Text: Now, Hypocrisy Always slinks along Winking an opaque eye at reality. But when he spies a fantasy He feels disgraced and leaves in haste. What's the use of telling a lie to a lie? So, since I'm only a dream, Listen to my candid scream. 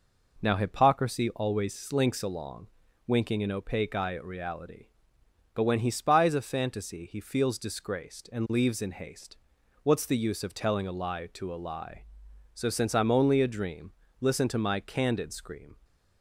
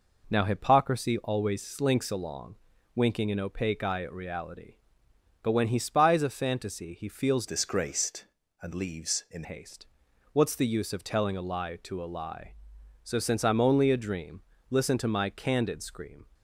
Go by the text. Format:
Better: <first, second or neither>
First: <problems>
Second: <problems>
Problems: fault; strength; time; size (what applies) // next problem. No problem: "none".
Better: first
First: pauses between "along" and "Winking"; at 2.6 s; 0.38 s long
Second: pauses between "along" and "Winking"; at 2.5 s; 0.38 s long // changes voice from "disgraced" to "in"; from 7.4 to 9.4 s; 2.0 s long